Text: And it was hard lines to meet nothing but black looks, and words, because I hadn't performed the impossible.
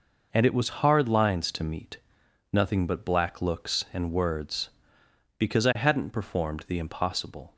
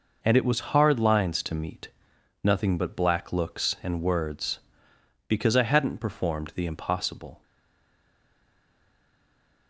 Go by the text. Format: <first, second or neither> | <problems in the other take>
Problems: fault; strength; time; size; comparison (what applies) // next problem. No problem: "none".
first | pauses between "meet" and "nothing"; noticeable; at 1.8 s; 0.54 s long; noticeable in the first // stays silent after the last word; from 7.4 s on; 2.2 s long